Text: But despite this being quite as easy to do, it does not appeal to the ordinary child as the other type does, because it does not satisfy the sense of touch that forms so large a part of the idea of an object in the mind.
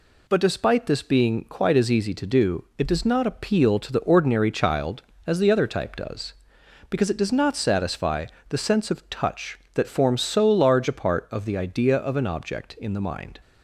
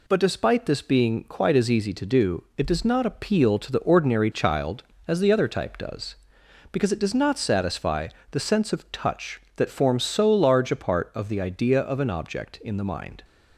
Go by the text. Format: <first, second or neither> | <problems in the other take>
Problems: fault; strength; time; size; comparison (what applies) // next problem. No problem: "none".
neither | pauses between "satisfy" and "the"; slight; the same in both